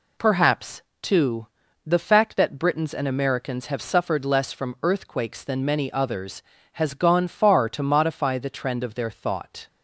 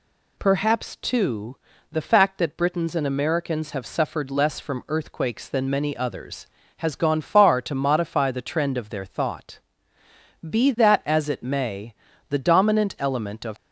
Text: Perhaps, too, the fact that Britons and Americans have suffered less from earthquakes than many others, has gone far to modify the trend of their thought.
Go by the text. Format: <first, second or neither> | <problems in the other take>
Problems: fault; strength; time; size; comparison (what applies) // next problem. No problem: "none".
first | goes on to say "Be that as it may the dominant element of"; strong; from 10.4 s on; 3.0 s long